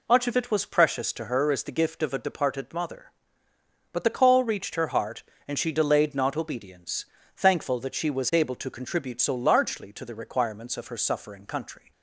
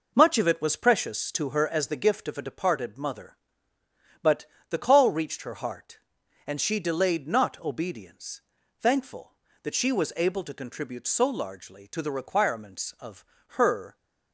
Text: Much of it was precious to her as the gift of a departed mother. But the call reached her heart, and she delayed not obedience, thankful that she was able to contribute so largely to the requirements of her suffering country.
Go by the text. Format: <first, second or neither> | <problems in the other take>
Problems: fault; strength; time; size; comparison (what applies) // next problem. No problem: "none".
first | pauses between "But" and "the"; slight; at 4.4 s; 0.24 s long // pauses between "of" and "her"; slight; at 13.2 s; 0.22 s long // stops before "suffering country"; at 13.9 s